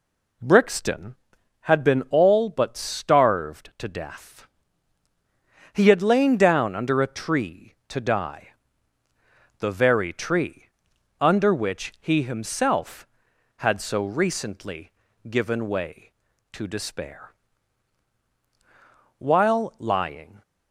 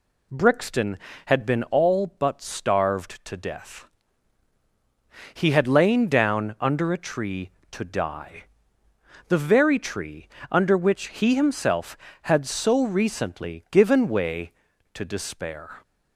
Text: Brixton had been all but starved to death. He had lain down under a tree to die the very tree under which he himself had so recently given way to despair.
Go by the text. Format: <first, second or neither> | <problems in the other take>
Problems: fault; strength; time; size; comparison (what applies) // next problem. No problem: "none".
second | pauses between "die" and "the"; at 8.4 s; 1.1 s long; noticeable in the second // pauses between "tree" and "under"; noticeable; at 10.6 s; 0.54 s long; slight in the second // pauses between "recently" and "given"; at 14.9 s; 0.38 s long // goes on to say "While lying"; noticeable; from 19.1 s on; 1.2 s long